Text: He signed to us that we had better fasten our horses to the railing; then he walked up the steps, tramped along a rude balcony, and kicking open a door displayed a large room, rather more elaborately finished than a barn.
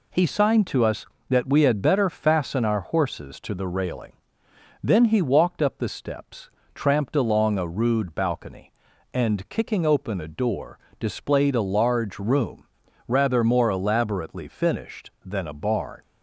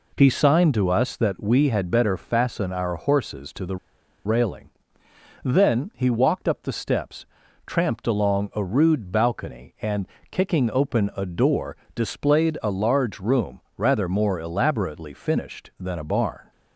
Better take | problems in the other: first | pauses between "the" and "railing"; noticeable; at 3.7 s; 0.49 s long // pauses between "and" and "kicking"; slight; at 10.0 s; 0.22 s long // pauses between "door" and "displayed"; slight; at 11.7 s; 0.18 s long; slight in the first

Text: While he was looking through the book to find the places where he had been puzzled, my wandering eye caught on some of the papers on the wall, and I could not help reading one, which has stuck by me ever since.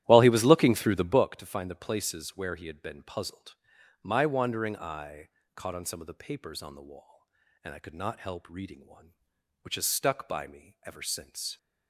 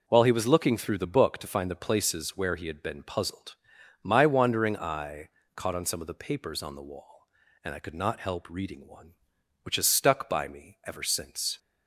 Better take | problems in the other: second | starts louder than the rest; strong; until 1.2 s; 13.5 dB // pauses between "eye" and "caught"; slight; at 5.2 s; 0.26 s long; slight in the second

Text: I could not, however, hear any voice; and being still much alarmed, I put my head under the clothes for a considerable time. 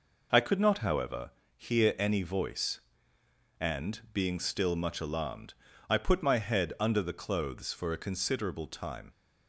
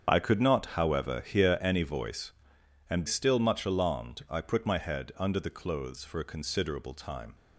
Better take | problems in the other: first | starts louder than the rest; strong; until 1.1 s; 7.5 dB // skips "being"; at 3.0 s

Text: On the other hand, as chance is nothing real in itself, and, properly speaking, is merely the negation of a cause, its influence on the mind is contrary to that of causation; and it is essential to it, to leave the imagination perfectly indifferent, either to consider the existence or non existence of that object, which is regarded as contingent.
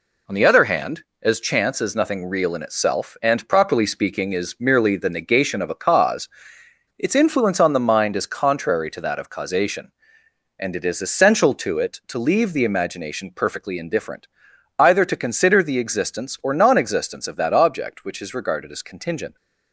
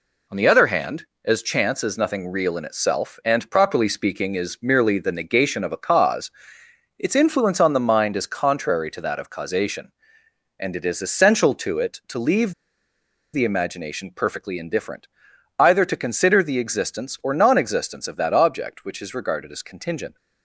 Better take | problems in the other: first | pauses between "leave" and "the"; noticeable; at 12.5 s; 0.80 s long

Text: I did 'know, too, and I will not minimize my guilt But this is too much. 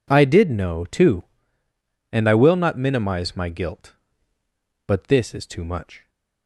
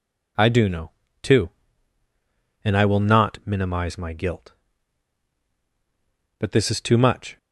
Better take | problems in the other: first | says "do" for "did"; at 0.4 s

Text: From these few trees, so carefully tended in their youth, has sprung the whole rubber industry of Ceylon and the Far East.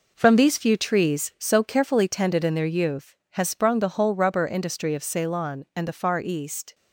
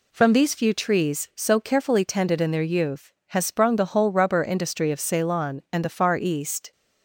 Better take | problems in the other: second | gets quieter; throughout; 6.5 dB

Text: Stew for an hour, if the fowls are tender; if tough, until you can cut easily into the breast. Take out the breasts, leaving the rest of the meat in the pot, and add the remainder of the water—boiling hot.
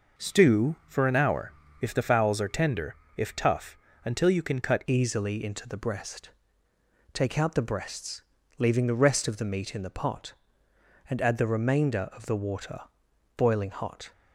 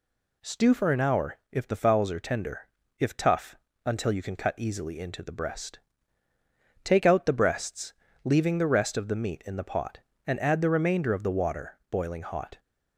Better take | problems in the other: second | changes voice at "easily"; from 4.8 s on; 9.3 s long

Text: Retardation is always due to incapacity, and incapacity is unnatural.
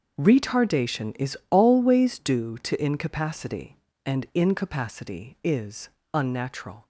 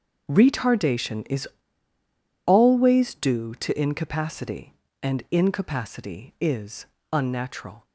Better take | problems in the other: first | starts louder than the rest; until 1.3 s; 6 dB; also in the first // pauses between "is" and "always"; at 1.4 s; 0.99 s long // pauses between "is" and "unnatural"; slight; at 6.8 s; 0.26 s long; slight in the first

